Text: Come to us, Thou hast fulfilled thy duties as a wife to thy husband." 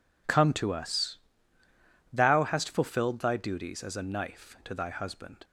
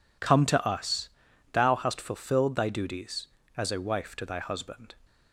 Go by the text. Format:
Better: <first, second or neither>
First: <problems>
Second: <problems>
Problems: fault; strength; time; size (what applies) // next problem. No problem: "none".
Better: second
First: says "knife" for "wife"; at 4.0 s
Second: none